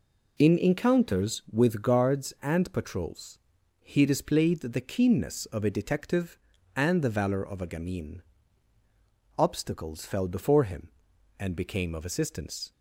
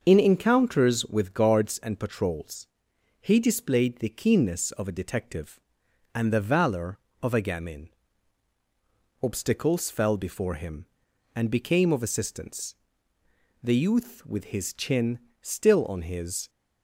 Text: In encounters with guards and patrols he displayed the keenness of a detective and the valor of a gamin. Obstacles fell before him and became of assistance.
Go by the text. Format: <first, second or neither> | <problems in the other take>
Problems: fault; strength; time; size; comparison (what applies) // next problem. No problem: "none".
first | starts louder than the rest; until 1.0 s; 6.5 dB // pauses between "patrols" and "he"; noticeable; at 2.6 s; 0.56 s long; also in the first // goes on to say "The youth with his chin still on his"; strong; from 13.6 s on; 2.8 s long